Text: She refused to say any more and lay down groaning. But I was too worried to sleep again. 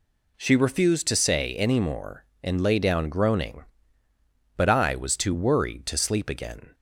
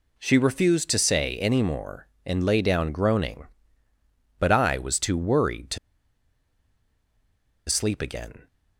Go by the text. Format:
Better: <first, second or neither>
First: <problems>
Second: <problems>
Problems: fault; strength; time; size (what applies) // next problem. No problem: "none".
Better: first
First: none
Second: pauses between "to" and "sleep"; strong; at 5.7 s; 1.9 s long